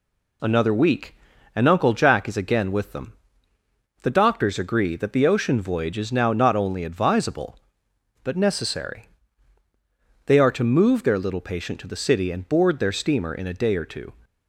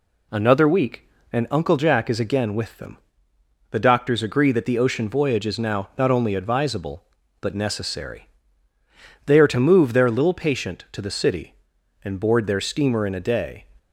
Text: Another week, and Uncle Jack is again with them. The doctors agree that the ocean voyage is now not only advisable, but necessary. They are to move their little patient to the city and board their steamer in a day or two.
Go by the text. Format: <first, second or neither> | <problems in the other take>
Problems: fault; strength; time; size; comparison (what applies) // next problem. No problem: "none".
first | stops before "or two"; at 13.7 s